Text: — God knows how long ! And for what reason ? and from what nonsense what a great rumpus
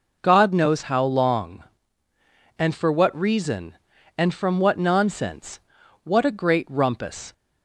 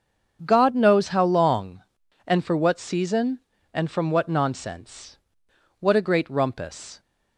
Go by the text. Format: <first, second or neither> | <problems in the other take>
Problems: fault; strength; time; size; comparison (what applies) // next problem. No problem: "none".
first | starts louder than the rest; strong; until 1.4 s; 7.5 dB // says "season" for "reason"; at 2.7 s // pauses between "nonsense" and "what"; noticeable; at 5.1 s; 0.64 s long; also in the first